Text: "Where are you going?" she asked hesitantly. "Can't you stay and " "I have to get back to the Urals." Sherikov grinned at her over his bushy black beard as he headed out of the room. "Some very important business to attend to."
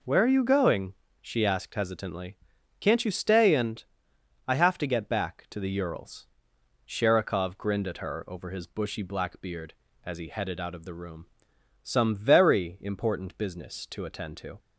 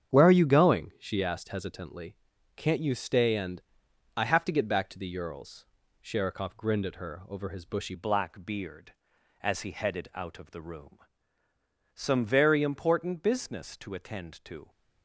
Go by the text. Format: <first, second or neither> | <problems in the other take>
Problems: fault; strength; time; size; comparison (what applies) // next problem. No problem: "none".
first | starts louder than the rest; strong; until 1.1 s; 8.5 dB // changes voice at "black"; from 7.9 s on; 6.7 s long